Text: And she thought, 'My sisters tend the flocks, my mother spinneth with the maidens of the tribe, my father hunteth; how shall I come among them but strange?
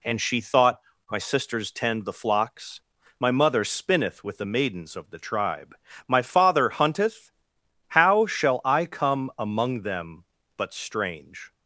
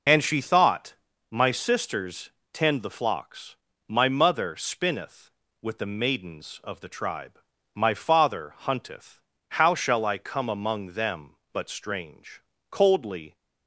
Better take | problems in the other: first | pauses between "sisters" and "tend"; slight; at 2.2 s; 0.24 s long // goes on to say "Coldly"; noticeable; from 12.7 s on; 0.64 s long

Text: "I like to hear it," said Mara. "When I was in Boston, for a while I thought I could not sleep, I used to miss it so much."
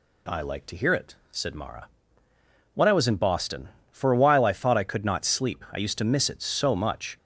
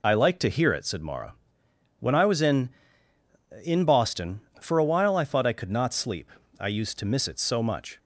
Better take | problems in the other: first | says "in" twice; at 3.6 s

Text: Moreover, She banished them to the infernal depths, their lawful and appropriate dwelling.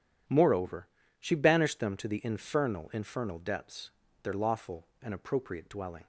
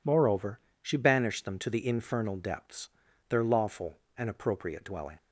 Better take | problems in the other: second | says "infernal" twice; at 2.9 s

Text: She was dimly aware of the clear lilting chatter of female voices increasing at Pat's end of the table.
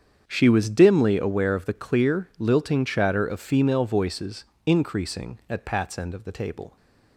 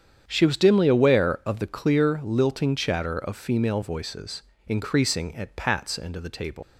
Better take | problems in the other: first | starts louder than the rest; strong; until 1.2 s; 8.5 dB; strong in the first // pauses between "voices" and "increasing"; slight; at 4.4 s; 0.26 s long; slight in the first // leaves "table" unfinished; at 6.6 s; 125 ms

